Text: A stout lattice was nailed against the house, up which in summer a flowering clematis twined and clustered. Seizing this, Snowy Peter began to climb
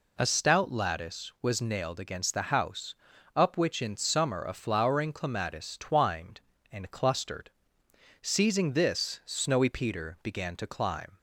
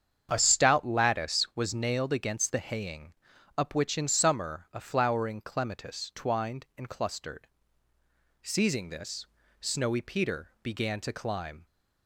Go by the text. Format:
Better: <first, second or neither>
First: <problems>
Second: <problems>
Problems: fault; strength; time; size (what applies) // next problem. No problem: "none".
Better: first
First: none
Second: starts louder than the rest; strong; until 1.3 s; 8 dB // says "haying" for "house"; at 2.5 s